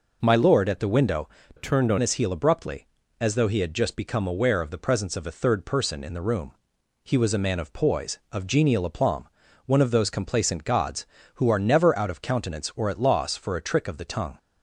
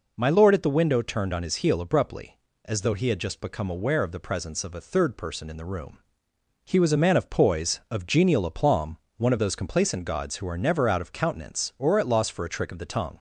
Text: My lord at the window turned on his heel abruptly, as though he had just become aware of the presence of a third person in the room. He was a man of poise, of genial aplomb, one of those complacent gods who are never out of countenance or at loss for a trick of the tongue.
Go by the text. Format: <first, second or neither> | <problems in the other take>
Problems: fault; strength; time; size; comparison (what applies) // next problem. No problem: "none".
second | changes voice from "turned" to "on"; from 1.5 to 1.9 s; 0.4 s long